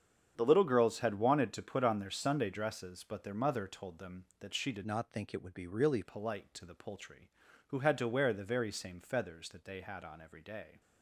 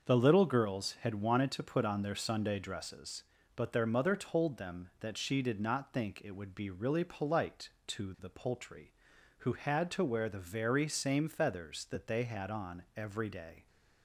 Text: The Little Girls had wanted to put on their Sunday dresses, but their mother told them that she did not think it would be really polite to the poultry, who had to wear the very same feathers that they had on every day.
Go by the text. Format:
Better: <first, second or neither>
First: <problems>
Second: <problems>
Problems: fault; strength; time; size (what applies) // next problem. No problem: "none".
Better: second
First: starts louder than the rest; strong; until 1.3 s; 8 dB // changes voice from "not" to "really"; from 4.8 to 6.0 s; 1.2 s long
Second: starts louder than the rest; until 1.1 s; 6.5 dB